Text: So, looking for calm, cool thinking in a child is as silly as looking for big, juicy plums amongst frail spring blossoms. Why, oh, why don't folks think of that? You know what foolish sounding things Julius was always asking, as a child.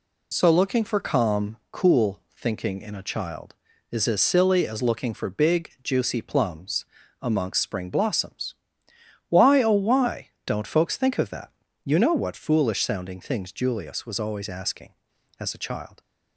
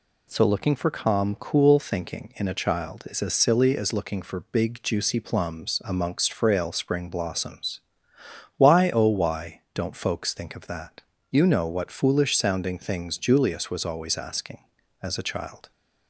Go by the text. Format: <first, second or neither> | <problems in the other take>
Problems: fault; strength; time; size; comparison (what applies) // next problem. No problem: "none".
second | pauses between "cool" and "thinking"; slight; at 2.1 s; 0.16 s long // pauses between "plums" and "amongst"; slight; at 6.8 s; 0.34 s long // skips "frail"; at 7.6 s // pauses between "why" and "don't"; slight; at 10.2 s; 0.18 s long